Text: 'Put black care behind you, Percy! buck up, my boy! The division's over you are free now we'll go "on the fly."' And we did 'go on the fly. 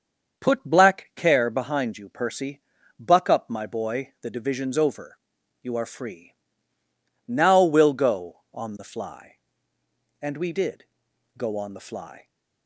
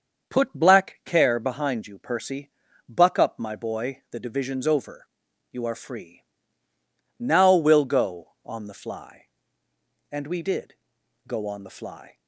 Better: neither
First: starts louder than the rest; until 1.4 s; 6.5 dB // pauses between "over" and "you"; noticeable; at 5.1 s; 0.46 s long // pauses between "free" and "now"; noticeable; at 6.3 s; 0.94 s long // pauses between "did" and "go"; noticeable; at 10.8 s; 0.52 s long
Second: starts louder than the rest; until 1.3 s; 6.5 dB // pauses between "over" and "you"; noticeable; at 5.0 s; 0.46 s long // pauses between "free" and "now"; noticeable; at 6.2 s; 0.96 s long // pauses between "did" and "go"; noticeable; at 10.7 s; 0.52 s long

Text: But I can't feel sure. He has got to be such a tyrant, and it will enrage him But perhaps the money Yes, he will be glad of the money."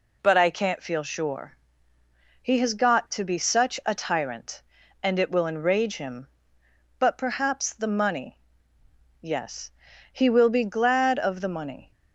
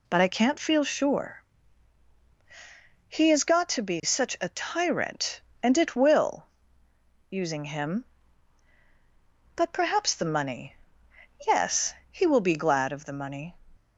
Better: first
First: pauses between "money" and "Yes"; noticeable; at 8.3 s; 0.80 s long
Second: says "using" for "enrage"; at 7.2 s // pauses between "money" and "Yes"; noticeable; at 10.7 s; 0.70 s long

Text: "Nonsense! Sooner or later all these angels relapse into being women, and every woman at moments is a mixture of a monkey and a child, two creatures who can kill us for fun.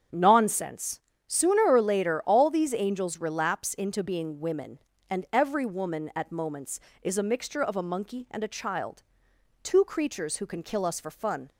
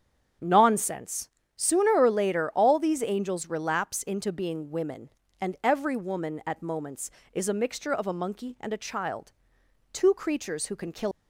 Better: first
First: starts louder than the rest; strong; until 1.3 s; 8 dB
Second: starts louder than the rest; strong; until 1.6 s; 8 dB // stops before "us for fun"; at 11.1 s

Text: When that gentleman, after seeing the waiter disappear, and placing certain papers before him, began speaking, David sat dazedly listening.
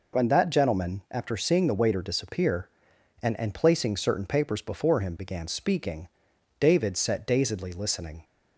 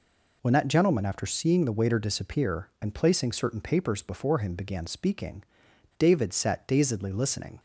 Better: second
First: says "and" twice; at 3.3 s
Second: none

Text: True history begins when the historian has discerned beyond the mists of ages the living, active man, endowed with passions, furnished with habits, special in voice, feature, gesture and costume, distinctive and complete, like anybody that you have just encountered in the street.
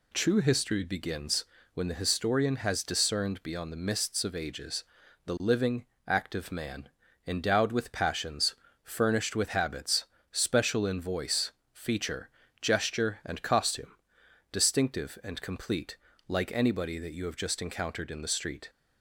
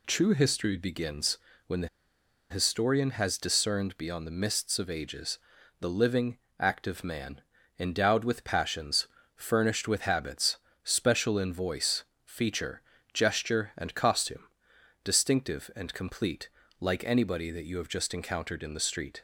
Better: first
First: pauses between "begins" and "when"; slight; at 1.4 s; 0.28 s long // pauses between "ages" and "the"; at 4.8 s; 0.42 s long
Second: pauses between "begins" and "when"; slight; at 1.3 s; 0.28 s long // pauses between "the" and "historian"; noticeable; at 1.8 s; 0.63 s long // pauses between "ages" and "the"; at 5.3 s; 0.42 s long

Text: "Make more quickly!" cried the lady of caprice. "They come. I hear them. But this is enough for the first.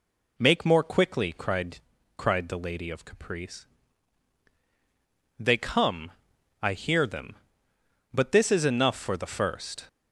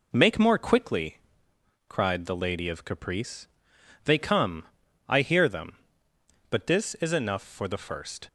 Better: second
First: says "cried" twice; at 2.1 s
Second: none

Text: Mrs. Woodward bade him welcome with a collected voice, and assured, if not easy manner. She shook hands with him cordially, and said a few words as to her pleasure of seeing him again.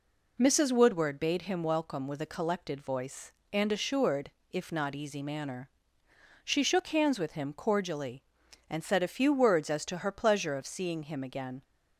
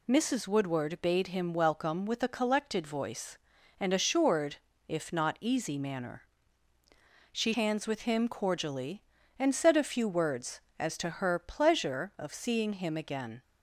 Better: first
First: none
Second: skips "shook"; at 7.5 s

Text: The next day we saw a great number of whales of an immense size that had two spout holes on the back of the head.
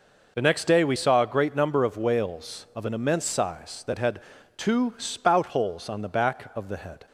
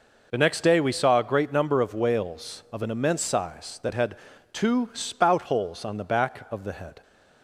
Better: neither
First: pauses between "had" and "two"; at 4.2 s; 0.38 s long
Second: pauses between "had" and "two"; at 4.1 s; 0.38 s long

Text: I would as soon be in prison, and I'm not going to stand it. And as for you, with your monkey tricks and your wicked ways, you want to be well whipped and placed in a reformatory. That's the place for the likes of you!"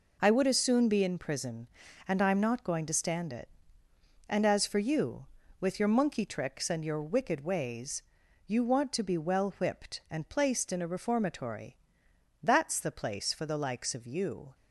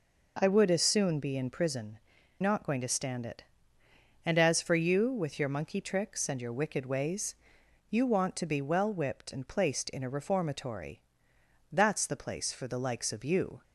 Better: first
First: none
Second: skips "and I'm"; at 2.1 s

